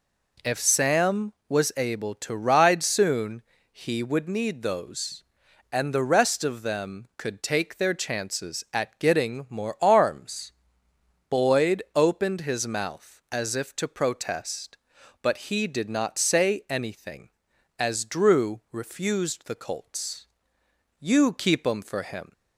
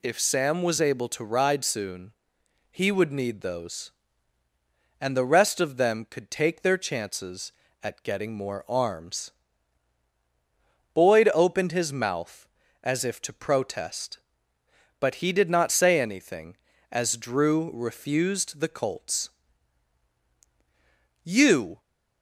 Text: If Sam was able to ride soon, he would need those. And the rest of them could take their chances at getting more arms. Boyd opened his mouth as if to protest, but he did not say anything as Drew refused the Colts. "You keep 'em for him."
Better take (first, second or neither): first